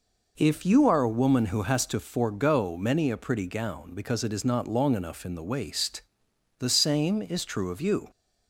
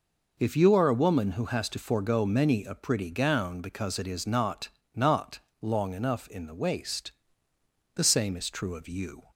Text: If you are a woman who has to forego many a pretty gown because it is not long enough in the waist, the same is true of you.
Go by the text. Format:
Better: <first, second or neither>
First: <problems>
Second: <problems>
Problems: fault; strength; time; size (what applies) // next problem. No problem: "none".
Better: first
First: none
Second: says "not" twice; at 4.9 s